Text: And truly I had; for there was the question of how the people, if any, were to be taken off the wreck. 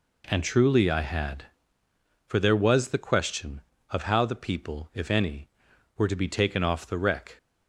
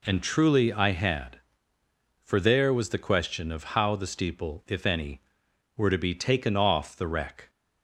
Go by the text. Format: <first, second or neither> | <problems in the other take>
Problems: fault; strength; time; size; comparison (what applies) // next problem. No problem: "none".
first | says "steeple" for "people"; at 4.0 s